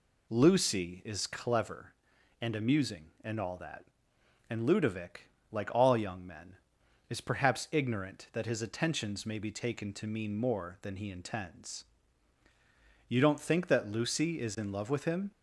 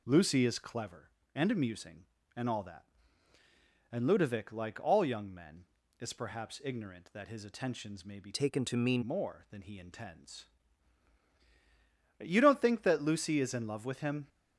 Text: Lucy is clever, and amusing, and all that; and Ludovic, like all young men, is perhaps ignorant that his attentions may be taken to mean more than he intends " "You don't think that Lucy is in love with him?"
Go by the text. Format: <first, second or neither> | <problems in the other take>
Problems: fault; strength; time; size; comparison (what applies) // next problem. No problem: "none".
first | changes voice from "taken" to "mean"; from 8.3 to 9.0 s; 0.7 s long